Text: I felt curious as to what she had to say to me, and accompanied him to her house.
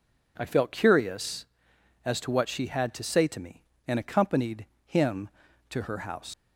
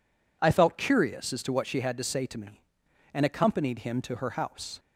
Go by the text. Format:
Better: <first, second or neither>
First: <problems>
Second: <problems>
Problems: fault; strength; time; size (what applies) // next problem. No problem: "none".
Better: second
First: pauses between "accompanied" and "him"; slight; at 4.6 s; 0.20 s long // leaves "house" unfinished; at 6.3 s; 125 ms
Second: none